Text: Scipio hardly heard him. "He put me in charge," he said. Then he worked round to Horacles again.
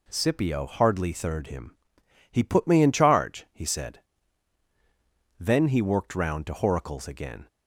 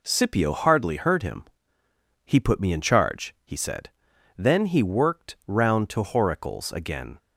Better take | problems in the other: second | says "third" for "heard"; at 1.1 s

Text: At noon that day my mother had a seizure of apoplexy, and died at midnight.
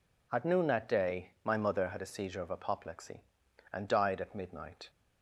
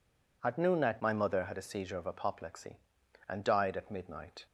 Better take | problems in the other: first | skips "day"; at 1.0 s

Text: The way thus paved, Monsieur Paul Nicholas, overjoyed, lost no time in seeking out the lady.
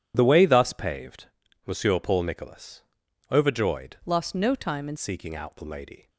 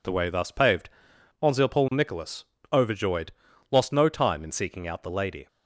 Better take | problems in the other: second | changes voice from "lost" to "in"; from 4.0 to 4.9 s; 0.9 s long

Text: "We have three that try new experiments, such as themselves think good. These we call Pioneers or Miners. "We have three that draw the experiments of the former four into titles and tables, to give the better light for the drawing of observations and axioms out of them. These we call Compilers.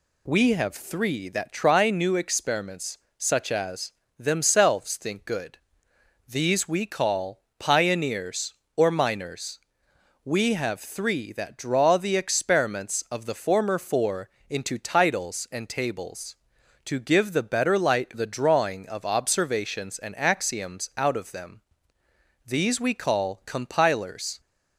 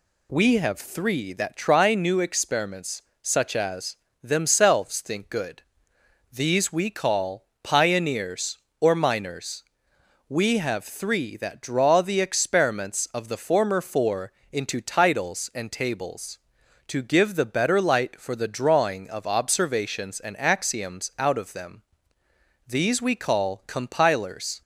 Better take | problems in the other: second | pauses between "as" and "themselves"; slight; at 3.9 s; 0.26 s long; slight in the second // pauses between "call" and "Pioneers"; slight; at 7.4 s; 0.16 s long; slight in the second // pauses between "four" and "into"; slight; at 14.2 s; 0.20 s long; slight in the second // skips "for"; at 18.1 s

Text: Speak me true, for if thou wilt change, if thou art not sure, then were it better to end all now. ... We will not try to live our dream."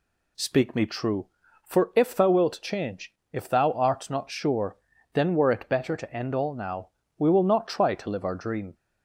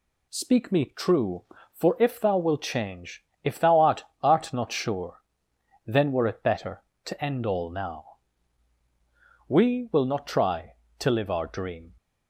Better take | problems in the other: first | says "art" twice; at 4.2 s

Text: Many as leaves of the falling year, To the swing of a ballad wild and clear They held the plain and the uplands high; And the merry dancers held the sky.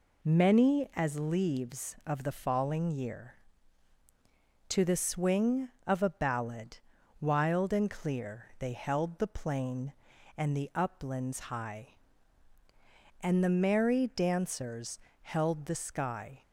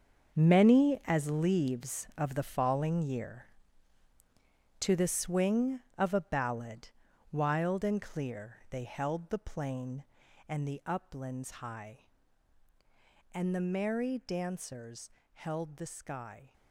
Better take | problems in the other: first | gets quieter; strong; throughout; 12.5 dB // pauses between "ballad" and "wild"; at 6.8 s; 0.44 s long; also in the first // pauses between "dancers" and "held"; slight; at 15.1 s; 0.22 s long; slight in the first

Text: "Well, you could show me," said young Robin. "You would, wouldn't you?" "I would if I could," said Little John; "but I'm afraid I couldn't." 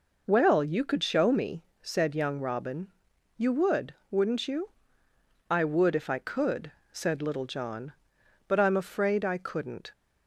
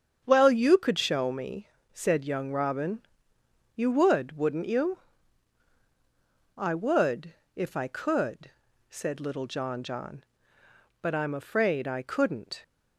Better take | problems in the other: first | starts louder than the rest; strong; until 1.2 s; 7.5 dB // pauses between "would" and "if"; slight; at 7.3 s; 0.24 s long // says "John" twice; at 9.8 s

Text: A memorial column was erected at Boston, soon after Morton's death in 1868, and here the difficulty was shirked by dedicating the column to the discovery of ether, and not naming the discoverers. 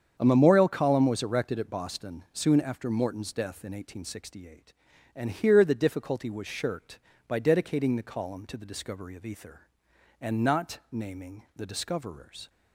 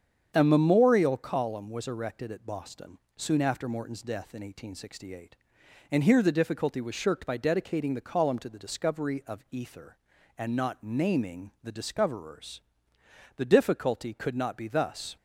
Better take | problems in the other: first | starts louder than the rest; strong; until 1.3 s; 7.5 dB; strong in the first // goes on to say "The difficulty could not be thus"; strong; from 13.3 s on; 1.8 s long

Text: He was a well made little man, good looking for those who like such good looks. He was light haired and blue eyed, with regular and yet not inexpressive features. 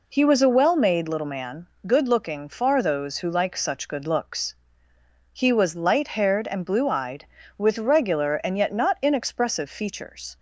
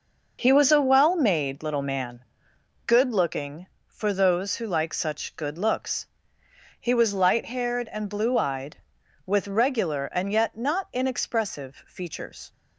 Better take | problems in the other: second | says "far" for "for"; at 2.4 s

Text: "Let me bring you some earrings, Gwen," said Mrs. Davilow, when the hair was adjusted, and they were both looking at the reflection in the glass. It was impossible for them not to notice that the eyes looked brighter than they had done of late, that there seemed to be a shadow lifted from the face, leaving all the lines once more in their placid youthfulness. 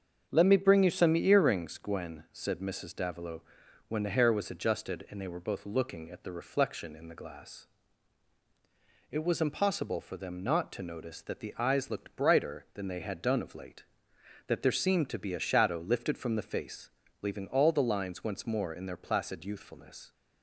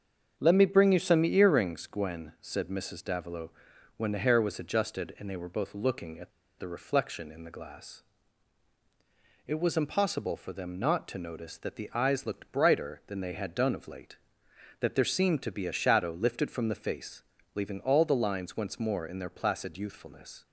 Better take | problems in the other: first | starts louder than the rest; until 1.3 s; 7 dB; also in the first // pauses between "at" and "the"; slight; at 6.3 s; 0.28 s long

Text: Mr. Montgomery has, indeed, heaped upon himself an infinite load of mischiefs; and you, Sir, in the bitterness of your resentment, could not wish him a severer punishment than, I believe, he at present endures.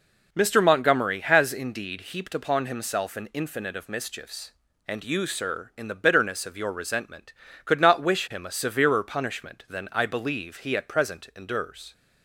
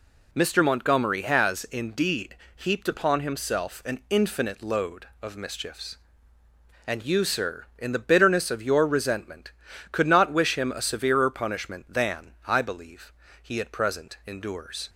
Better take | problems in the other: second | skips "load"; at 3.7 s

